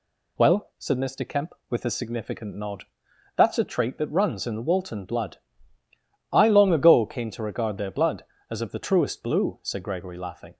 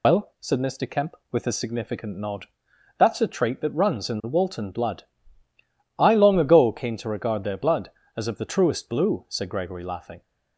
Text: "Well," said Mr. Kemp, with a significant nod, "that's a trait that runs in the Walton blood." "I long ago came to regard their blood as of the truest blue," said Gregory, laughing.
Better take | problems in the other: first | loses the start of "Well"; at 0.0 s; 50 ms

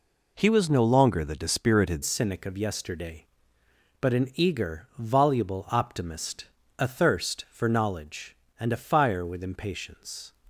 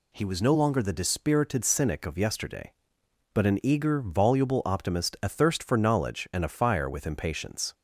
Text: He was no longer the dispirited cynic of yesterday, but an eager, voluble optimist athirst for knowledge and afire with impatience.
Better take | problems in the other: second | changes voice at "cynic"; from 2.0 s on; 8.3 s long // pauses between "optimist" and "athirst"; slight; at 6.4 s; 0.34 s long

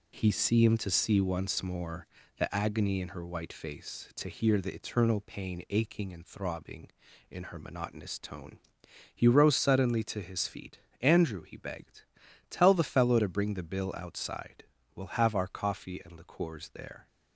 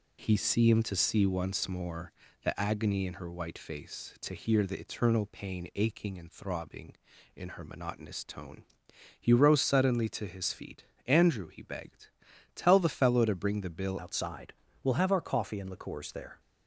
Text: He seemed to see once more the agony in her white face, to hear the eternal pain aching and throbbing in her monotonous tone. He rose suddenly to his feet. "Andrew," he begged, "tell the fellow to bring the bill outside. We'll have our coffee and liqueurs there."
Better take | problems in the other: first | pauses between "more" and "the"; slight; at 2.1 s; 0.32 s long; slight in the first // changes voice at "outside"; from 13.9 s on; 2.4 s long

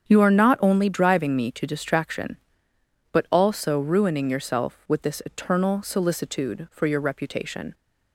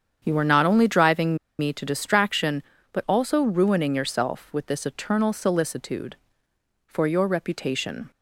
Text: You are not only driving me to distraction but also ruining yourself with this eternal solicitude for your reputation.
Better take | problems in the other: first | starts louder than the rest; strong; until 1.2 s; 8 dB; strong in the first // pauses between "driving" and "me"; slight; at 1.3 s; 0.21 s long

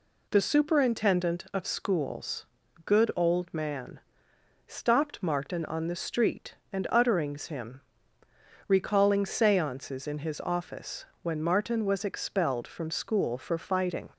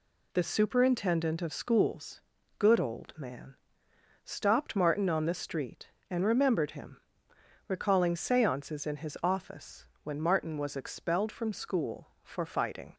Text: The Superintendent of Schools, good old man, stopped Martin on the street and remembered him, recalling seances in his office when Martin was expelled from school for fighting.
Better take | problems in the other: second | says "utterings" for "remembered"; at 6.8 s // pauses between "office" and "when"; slight; at 11.0 s; 0.16 s long; slight in the second

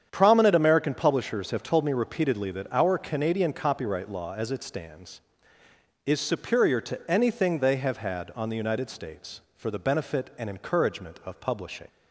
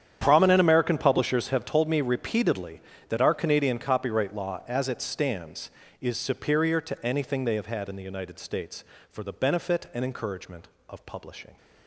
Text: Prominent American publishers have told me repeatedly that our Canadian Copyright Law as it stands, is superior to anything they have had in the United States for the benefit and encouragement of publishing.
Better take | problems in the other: second | starts louder than the rest; strong; until 1.1 s; 8.5 dB; strong in the second // says "on" for "in"; at 8.3 s

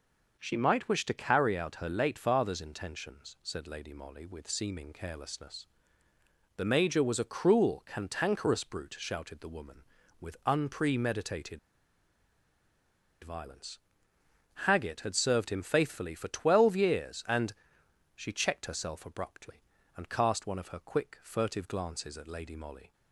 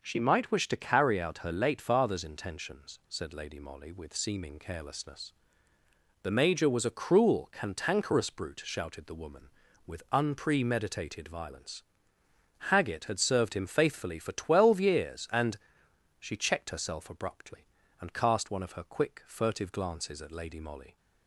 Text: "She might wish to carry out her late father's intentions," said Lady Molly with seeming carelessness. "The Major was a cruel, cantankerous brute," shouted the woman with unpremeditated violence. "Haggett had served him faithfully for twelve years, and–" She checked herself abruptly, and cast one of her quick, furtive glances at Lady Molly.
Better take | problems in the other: second | pauses between "unpremeditated" and "violence"; strong; at 11.5 s; 1.6 s long

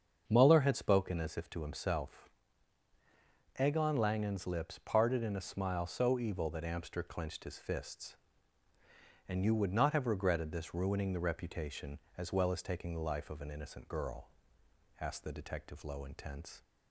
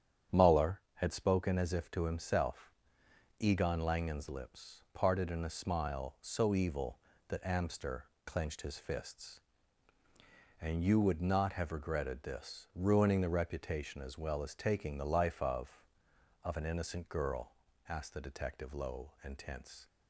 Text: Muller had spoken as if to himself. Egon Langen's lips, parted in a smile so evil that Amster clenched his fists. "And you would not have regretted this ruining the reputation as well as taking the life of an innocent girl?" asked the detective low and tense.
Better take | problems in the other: first | starts louder than the rest; strong; until 1.4 s; 9 dB; also in the first // pauses between "Amster" and "clenched"; slight; at 8.0 s; 0.20 s long // says "of" twice; at 16.4 s

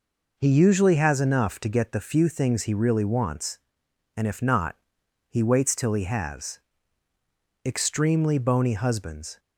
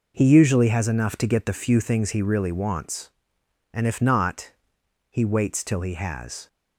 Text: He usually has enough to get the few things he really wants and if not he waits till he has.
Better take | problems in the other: second | pauses between "not" and "he"; noticeable; at 4.7 s; 0.54 s long; noticeable in the second // goes on to say "Extremely bony husbands"; strong; from 7.6 s on; 1.7 s long

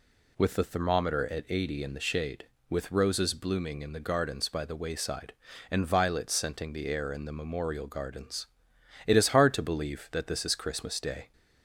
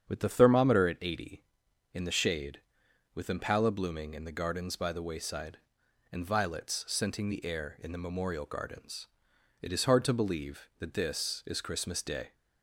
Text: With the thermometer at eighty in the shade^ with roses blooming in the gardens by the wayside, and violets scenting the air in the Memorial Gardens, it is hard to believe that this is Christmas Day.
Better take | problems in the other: first | starts louder than the rest; strong; until 1.1 s; 8 dB // says "impala" for "roses"; at 3.2 s

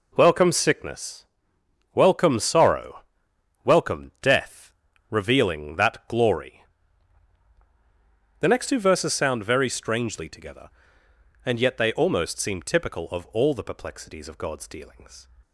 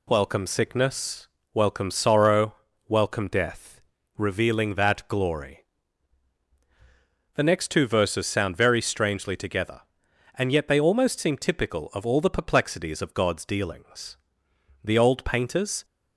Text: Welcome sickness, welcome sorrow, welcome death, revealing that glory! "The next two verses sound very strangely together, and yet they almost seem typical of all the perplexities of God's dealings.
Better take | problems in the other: first | goes on to say "The old painters"; noticeable; from 14.8 s on; 1.0 s long

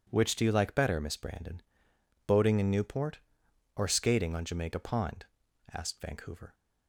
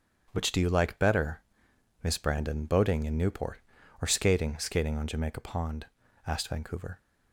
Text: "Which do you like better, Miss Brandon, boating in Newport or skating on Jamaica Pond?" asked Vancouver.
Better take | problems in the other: first | starts louder than the rest; strong; until 1.3 s; 8 dB // says "skating" twice; at 4.5 s

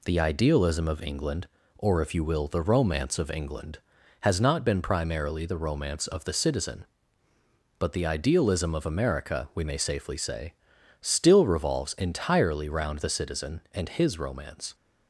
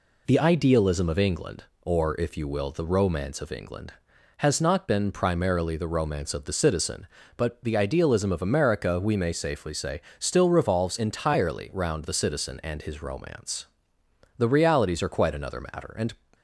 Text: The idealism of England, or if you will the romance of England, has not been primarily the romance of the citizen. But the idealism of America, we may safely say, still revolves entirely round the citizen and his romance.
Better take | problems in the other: first | goes on to say "The realities are quite another matter and"; strong; from 14.3 s on; 1.7 s long

